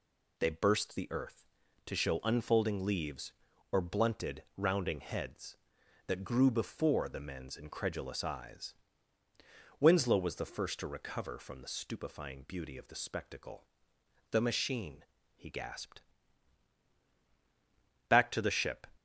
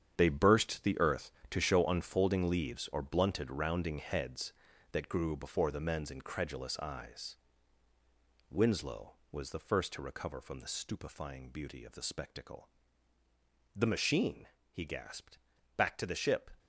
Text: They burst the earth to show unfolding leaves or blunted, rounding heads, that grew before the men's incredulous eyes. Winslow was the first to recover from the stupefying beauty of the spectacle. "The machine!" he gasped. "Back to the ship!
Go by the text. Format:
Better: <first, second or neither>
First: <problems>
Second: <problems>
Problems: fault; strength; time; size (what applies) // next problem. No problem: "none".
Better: first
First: none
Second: gets quieter; strong; throughout; 11 dB